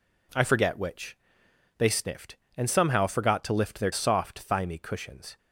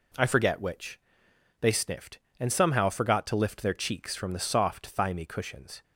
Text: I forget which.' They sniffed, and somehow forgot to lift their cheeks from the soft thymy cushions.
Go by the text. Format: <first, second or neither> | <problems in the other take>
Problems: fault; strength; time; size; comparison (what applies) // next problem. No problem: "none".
second | skips "cheeks from the"; at 3.9 s